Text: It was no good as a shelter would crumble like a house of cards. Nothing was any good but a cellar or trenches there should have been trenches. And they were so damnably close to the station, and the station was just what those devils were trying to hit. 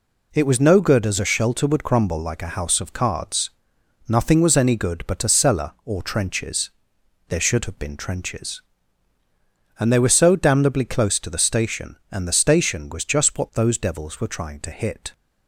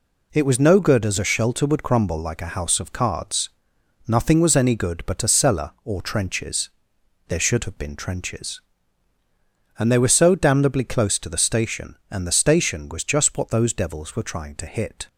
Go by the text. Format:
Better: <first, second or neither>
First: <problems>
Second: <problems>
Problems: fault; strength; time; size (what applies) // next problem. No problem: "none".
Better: neither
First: pauses between "trenches" and "there"; noticeable; at 6.7 s; 0.58 s long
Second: pauses between "trenches" and "there"; noticeable; at 6.6 s; 0.58 s long